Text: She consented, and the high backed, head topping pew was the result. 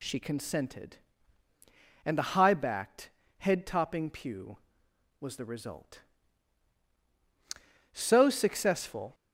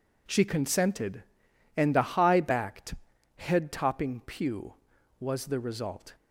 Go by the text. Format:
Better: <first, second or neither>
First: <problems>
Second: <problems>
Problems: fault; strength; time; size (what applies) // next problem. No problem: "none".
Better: second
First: goes on to say "So successful"; noticeable; from 7.9 s on; 1.2 s long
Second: none